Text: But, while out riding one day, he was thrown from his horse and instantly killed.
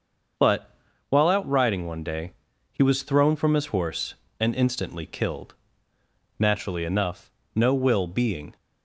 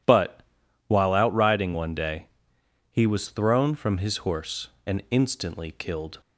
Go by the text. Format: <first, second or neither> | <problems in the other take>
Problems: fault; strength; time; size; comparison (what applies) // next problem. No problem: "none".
second | starts louder than the rest; until 1.7 s; 6 dB // goes on to say "Naturally enough no will being"; strong; from 6.3 s on; 2.1 s long